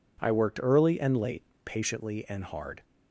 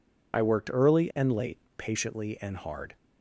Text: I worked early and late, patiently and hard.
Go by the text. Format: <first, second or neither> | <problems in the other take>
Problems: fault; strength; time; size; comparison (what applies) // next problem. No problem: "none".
first | loses the start of "I"; at 0.3 s; 55 ms